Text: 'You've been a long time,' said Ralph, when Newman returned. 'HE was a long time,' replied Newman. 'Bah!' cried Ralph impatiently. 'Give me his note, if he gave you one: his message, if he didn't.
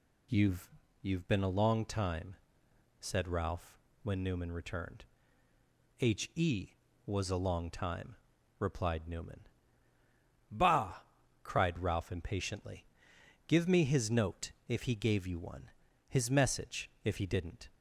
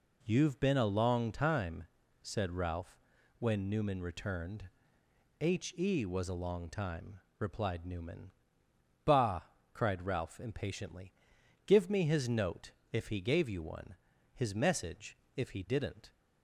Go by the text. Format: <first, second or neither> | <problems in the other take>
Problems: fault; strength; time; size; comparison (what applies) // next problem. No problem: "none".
second | says "You've" twice; at 1.0 s